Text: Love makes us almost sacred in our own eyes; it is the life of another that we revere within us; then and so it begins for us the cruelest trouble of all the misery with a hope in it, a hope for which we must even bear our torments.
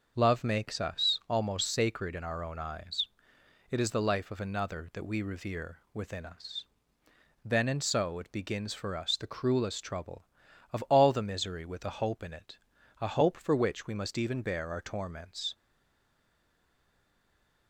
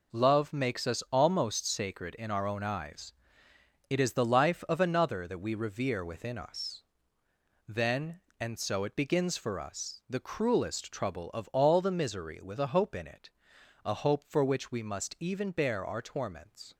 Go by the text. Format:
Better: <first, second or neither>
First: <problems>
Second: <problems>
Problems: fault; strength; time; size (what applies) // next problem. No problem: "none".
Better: second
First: starts louder than the rest; until 1.1 s; 6.5 dB // pauses between "revere" and "within"; slight; at 5.7 s; 0.16 s long // stays silent after the last word; from 15.5 s on; 2.1 s long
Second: none